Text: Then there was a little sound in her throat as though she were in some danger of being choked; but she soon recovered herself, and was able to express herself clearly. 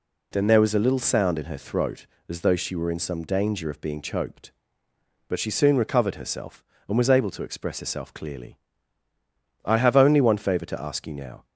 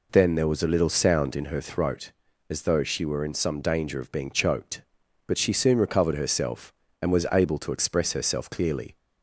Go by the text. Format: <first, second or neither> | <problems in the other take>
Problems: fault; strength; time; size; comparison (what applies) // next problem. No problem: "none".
second | goes on to say "I have only one favour to ask you now"; strong; from 9.6 s on; 1.8 s long